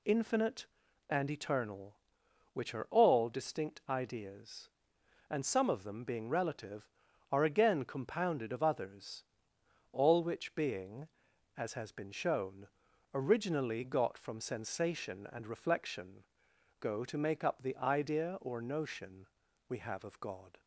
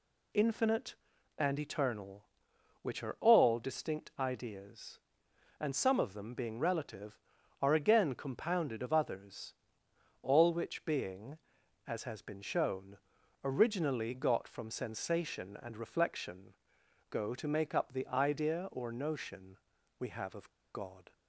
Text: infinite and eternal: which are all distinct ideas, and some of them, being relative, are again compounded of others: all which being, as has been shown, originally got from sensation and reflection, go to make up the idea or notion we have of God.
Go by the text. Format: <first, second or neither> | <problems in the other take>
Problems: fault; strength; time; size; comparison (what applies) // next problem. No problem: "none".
first | pauses between "notion" and "we"; at 19.5 s; 0.42 s long; also in the first // pauses between "of" and "God"; slight; at 20.4 s; 0.25 s long